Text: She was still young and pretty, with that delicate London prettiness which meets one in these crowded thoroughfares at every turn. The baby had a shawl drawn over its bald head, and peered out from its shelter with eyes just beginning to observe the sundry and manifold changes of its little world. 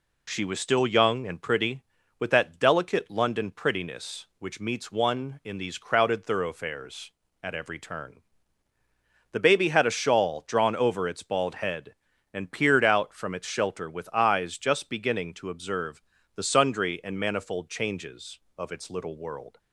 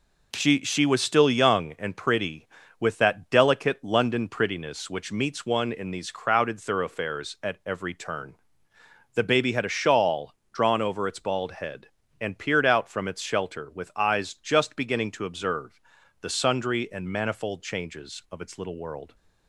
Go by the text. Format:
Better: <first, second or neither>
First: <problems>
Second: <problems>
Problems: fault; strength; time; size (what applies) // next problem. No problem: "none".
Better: first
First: pauses between "observe" and "the"; slight; at 16.0 s; 0.32 s long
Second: says "She" twice; at 0.6 s // pauses between "shawl" and "drawn"; slight; at 10.3 s; 0.20 s long // pauses between "observe" and "the"; at 15.8 s; 0.40 s long